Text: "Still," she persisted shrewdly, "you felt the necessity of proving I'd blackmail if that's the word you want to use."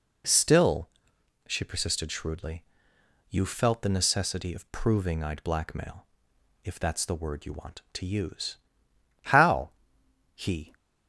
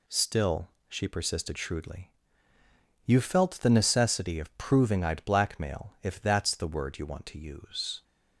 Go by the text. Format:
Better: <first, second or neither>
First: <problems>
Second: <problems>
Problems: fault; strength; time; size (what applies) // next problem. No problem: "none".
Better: second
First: pauses between "blackmail" and "if"; noticeable; at 6.0 s; 0.58 s long // goes on to say "How he"; from 9.3 s on; 1.4 s long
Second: none